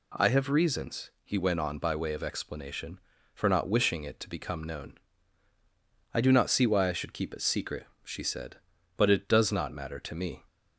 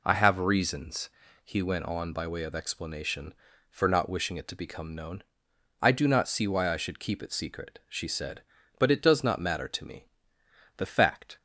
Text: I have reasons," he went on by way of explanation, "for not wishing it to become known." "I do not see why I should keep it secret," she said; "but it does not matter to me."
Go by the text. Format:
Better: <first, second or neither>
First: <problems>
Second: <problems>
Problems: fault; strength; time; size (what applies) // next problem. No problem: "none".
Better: first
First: none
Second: goes on to say "The fact"; from 10.7 s on; 0.60 s long